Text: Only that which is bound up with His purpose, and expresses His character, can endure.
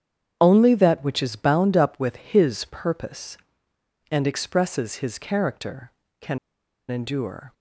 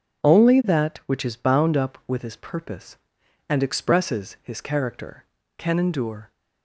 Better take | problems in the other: second | starts louder than the rest; strong; until 1.4 s; 8.5 dB // pauses between "can" and "endure"; noticeable; at 6.3 s; 0.50 s long

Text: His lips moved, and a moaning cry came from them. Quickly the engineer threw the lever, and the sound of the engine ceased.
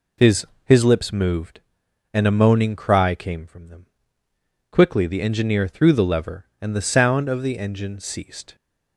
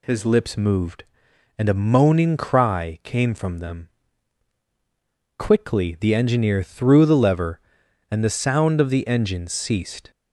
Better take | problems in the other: second | says "His" twice; at 0.6 s

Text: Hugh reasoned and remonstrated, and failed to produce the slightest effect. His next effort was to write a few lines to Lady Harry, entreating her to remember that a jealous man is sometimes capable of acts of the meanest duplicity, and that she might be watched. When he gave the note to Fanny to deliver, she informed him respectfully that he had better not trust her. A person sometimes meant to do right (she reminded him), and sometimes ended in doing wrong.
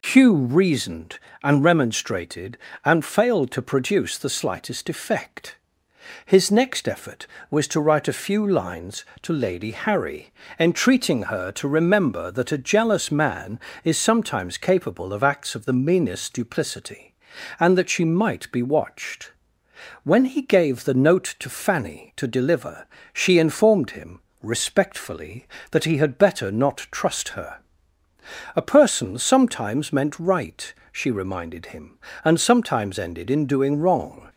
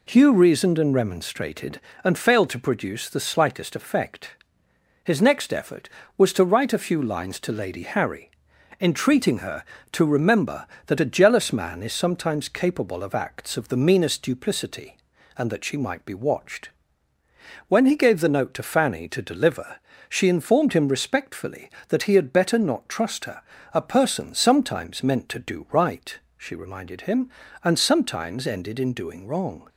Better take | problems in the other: second | pauses between "him" and "respectfully"; slight; at 24.2 s; 0.22 s long // skips "to do"; at 30.1 s

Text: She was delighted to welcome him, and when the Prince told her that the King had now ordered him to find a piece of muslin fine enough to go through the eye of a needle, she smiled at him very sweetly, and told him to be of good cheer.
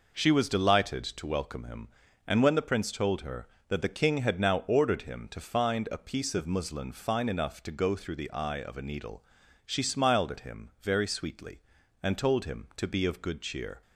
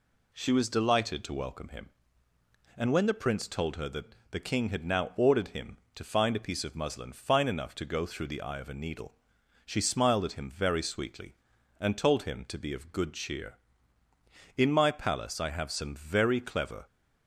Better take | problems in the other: first | goes on to say "In my palace I have some very clever"; strong; from 14.5 s on; 2.3 s long

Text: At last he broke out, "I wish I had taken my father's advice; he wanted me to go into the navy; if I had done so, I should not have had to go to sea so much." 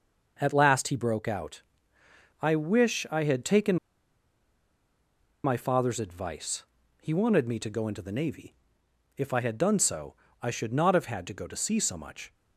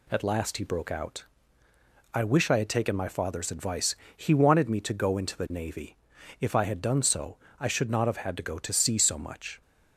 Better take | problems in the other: second | pauses between "taken" and "my"; strong; at 3.7 s; 1.6 s long

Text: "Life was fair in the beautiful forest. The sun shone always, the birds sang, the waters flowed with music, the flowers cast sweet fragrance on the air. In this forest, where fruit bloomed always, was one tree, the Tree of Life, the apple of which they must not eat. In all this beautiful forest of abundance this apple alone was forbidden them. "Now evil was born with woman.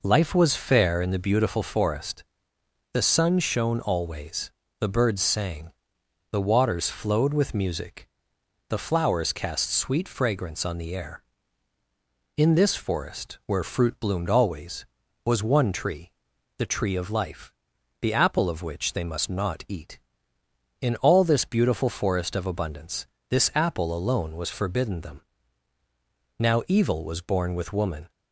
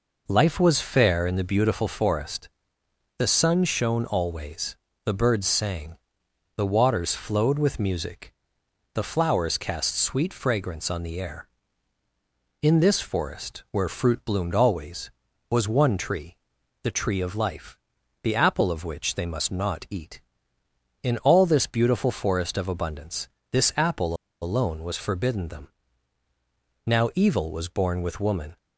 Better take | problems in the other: first | pauses between "abundance" and "this"; slight; at 23.2 s; 0.24 s long; slight in the first // pauses between "apple" and "alone"; slight; at 24.1 s; 0.26 s long

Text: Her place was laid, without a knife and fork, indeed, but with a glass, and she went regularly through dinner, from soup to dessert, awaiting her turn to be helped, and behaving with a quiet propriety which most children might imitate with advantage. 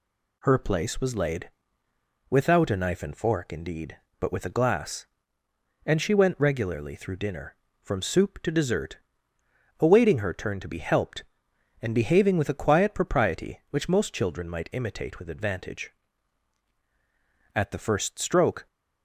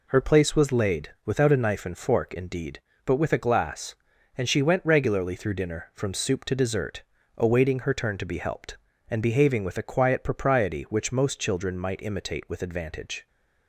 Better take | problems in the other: second | goes on to say "At the first stroke"; noticeable; from 17.5 s on; 1.1 s long

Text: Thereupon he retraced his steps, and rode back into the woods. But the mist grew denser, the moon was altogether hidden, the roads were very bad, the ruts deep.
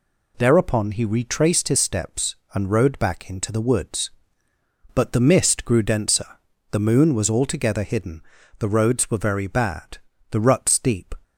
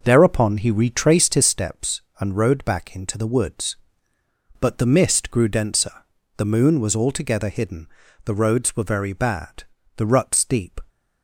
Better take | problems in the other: first | starts louder than the rest; noticeable; until 1.6 s; 6 dB

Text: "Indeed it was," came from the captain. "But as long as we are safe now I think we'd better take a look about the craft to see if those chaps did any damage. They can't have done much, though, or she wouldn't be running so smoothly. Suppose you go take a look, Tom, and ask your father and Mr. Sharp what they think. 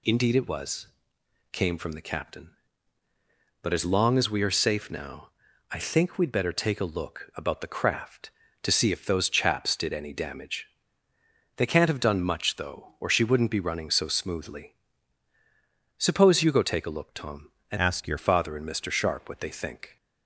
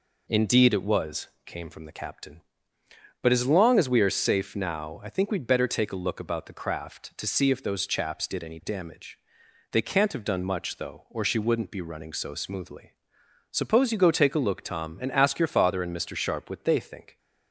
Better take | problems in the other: second | pauses between "now" and "I"; at 5.3 s; 0.40 s long // changes voice from "ask" to "your"; from 17.7 to 18.1 s; 0.4 s long

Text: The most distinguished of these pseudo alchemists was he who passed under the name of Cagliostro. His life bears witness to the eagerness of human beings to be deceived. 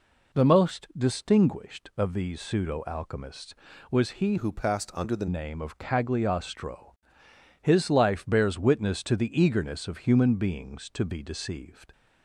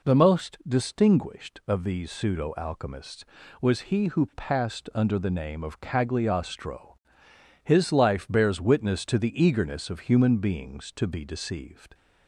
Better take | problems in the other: second | changes voice from "who" to "the"; from 4.3 to 5.2 s; 0.9 s long

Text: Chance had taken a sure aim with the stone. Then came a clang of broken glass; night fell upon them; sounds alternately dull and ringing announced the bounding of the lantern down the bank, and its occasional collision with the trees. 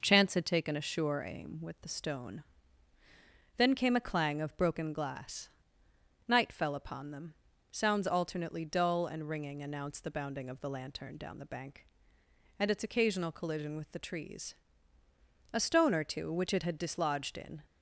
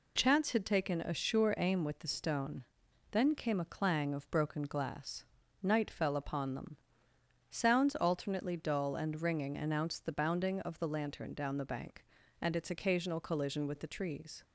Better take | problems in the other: second | goes on to say "A stone or two which it had dislodged in"; strong; from 15.5 s on; 2.0 s long

